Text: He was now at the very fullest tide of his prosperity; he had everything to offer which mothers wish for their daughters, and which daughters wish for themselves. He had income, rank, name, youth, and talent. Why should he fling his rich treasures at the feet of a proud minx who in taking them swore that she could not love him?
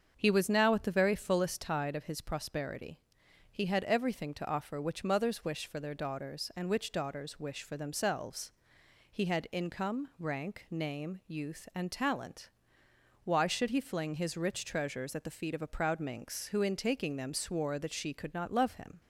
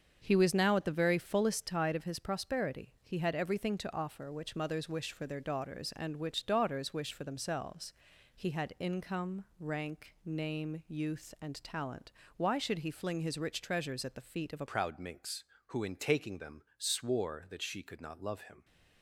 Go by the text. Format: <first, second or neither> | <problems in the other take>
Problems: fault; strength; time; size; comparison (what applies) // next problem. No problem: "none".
first | starts louder than the rest; until 1.2 s; 7 dB; also in the first // changes voice at "proud"; from 14.6 s on; 4.0 s long